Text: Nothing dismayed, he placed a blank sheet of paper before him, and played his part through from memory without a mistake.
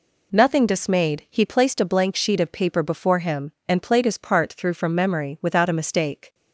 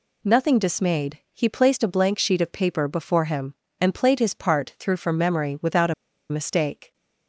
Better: first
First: none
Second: pauses between "a" and "mistake"; at 5.9 s; 0.36 s long

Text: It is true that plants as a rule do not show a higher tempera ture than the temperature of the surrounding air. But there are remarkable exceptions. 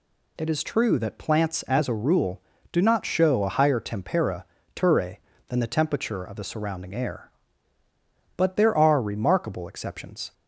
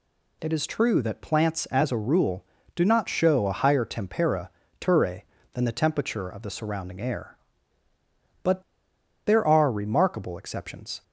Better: first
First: pauses between "tempera" and "ture"; slight; at 4.4 s; 0.30 s long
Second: pauses between "tempera" and "ture"; slight; at 4.4 s; 0.30 s long // pauses between "But" and "there"; noticeable; at 8.6 s; 0.63 s long

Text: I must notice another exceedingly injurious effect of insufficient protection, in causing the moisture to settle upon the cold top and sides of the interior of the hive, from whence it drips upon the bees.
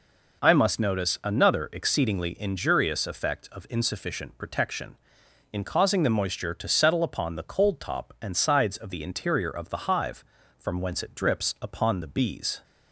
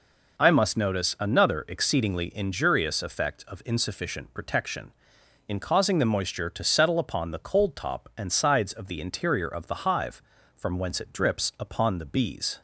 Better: neither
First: none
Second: none

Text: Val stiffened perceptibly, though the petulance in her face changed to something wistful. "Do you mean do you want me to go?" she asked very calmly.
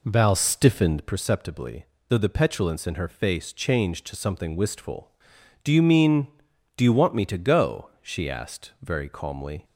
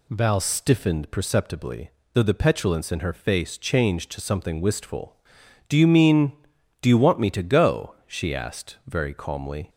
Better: second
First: starts louder than the rest; slight; until 1.1 s; 3 dB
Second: none

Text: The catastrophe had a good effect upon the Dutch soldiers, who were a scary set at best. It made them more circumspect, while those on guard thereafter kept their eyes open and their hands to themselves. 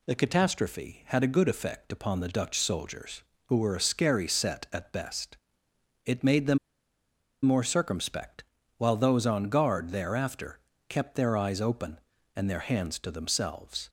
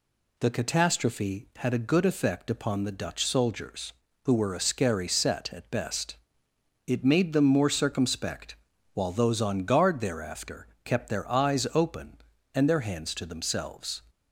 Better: second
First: pauses between "them" and "more"; noticeable; at 6.5 s; 0.84 s long // pauses between "thereafter" and "kept"; slight; at 10.5 s; 0.28 s long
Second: pauses between "thereafter" and "kept"; slight; at 10.6 s; 0.16 s long

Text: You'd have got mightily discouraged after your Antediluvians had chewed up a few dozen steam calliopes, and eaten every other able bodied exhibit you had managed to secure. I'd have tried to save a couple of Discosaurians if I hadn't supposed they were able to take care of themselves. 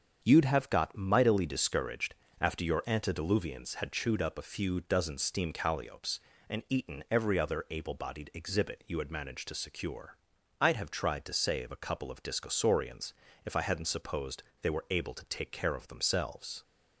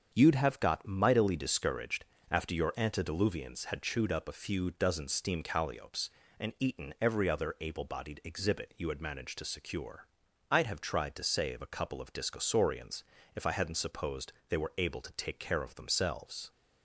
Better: neither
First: starts louder than the rest; strong; until 1.2 s; 7 dB // pauses between "discouraged" and "after"; slight; at 2.1 s; 0.26 s long // pauses between "Discosaurians" and "if"; slight; at 13.1 s; 0.32 s long // pauses between "supposed" and "they"; slight; at 14.4 s; 0.18 s long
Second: starts louder than the rest; strong; until 1.1 s; 7 dB // pauses between "discouraged" and "after"; slight; at 2.0 s; 0.26 s long // pauses between "Discosaurians" and "if"; slight; at 13.0 s; 0.32 s long // pauses between "supposed" and "they"; slight; at 14.3 s; 0.16 s long

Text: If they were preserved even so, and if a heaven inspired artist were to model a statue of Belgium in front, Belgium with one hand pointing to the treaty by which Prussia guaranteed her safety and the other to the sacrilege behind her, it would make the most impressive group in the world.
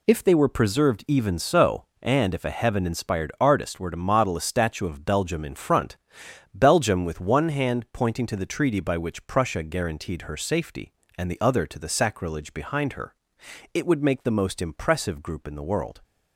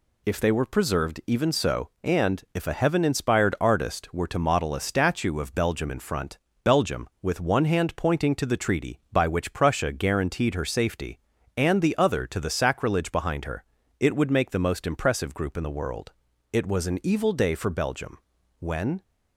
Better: first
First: none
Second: goes on to say "It was an evil day for Belgium when"; strong; from 16.5 s on; 2.5 s long

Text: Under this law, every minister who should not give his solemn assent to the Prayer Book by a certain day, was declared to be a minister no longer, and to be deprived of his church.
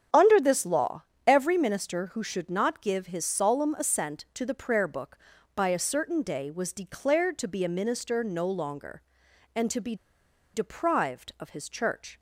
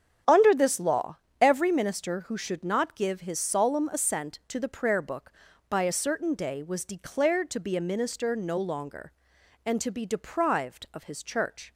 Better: second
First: starts louder than the rest; strong; until 1.3 s; 8 dB // pauses between "be" and "deprived"; noticeable; at 9.9 s; 0.59 s long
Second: starts louder than the rest; strong; until 1.4 s; 8 dB

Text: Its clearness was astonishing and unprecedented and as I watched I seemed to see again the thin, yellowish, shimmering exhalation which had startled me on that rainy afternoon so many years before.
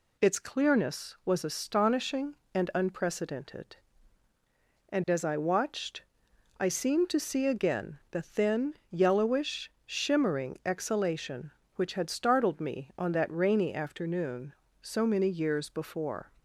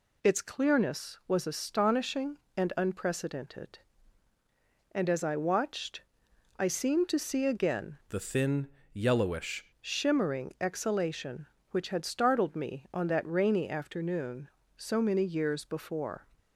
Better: first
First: pauses between "watched" and "I"; noticeable; at 6.0 s; 0.56 s long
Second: pauses between "watched" and "I"; noticeable; at 6.0 s; 0.56 s long // changes voice from "the" to "yellowish"; from 8.0 to 9.6 s; 1.6 s long

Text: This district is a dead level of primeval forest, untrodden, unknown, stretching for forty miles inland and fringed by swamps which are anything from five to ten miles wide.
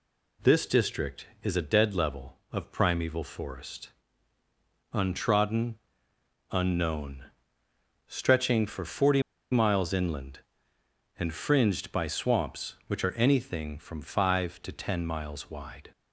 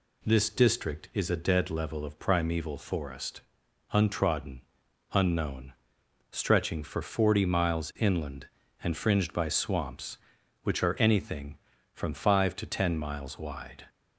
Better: second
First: pauses between "forty" and "miles"; slight; at 9.2 s; 0.29 s long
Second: none

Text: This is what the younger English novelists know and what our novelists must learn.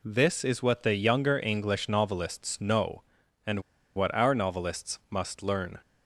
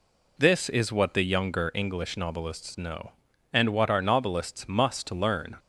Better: second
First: pauses between "and" and "what"; slight; at 3.6 s; 0.34 s long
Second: none

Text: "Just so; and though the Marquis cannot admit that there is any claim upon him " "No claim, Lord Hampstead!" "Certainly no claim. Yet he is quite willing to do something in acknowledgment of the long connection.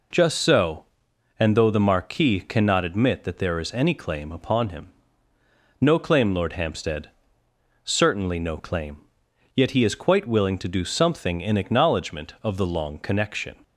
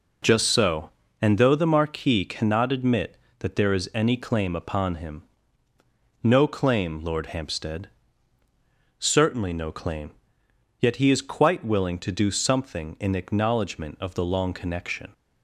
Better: neither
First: none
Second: none

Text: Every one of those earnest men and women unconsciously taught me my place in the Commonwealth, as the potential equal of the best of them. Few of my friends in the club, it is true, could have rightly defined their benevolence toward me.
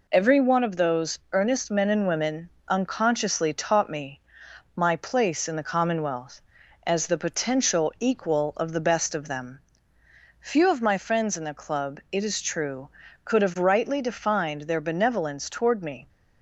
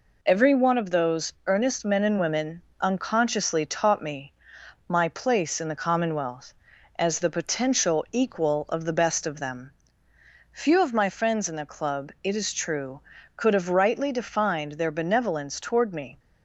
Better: neither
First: pauses between "women" and "unconsciously"; slight; at 2.4 s; 0.20 s long // pauses between "me" and "my"; noticeable; at 4.2 s; 0.52 s long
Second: pauses between "women" and "unconsciously"; slight; at 2.6 s; 0.20 s long // pauses between "me" and "my"; noticeable; at 4.3 s; 0.52 s long

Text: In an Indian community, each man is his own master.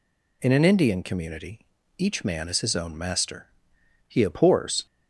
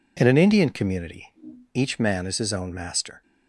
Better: second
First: goes on to say "He abhors"; noticeable; from 4.0 s on; 0.78 s long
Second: none

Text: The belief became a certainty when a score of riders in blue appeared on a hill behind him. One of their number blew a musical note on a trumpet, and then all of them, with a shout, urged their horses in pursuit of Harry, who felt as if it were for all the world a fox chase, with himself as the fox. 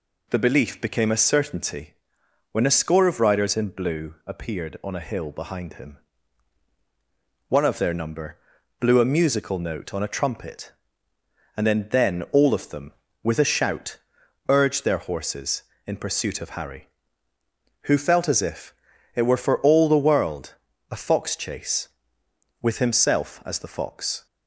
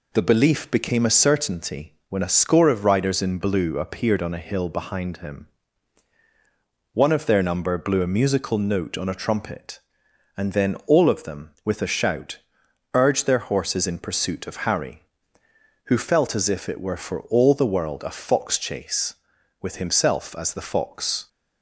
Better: second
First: pauses between "certainty" and "when"; noticeable; at 1.9 s; 0.58 s long // pauses between "number" and "blew"; at 8.3 s; 0.42 s long // says "then" twice; at 11.9 s // pauses between "if" and "it"; at 18.7 s; 0.42 s long // pauses between "world" and "a"; slight; at 20.5 s; 0.34 s long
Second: pauses between "certainty" and "when"; slight; at 1.9 s; 0.16 s long

